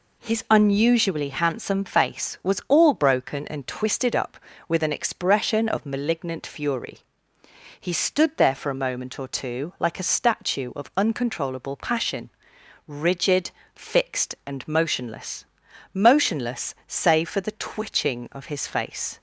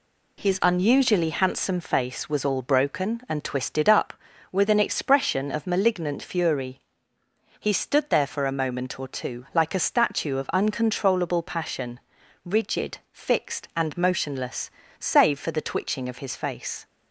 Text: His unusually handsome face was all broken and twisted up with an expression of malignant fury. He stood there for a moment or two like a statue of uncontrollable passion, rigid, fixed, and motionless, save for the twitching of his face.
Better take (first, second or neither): second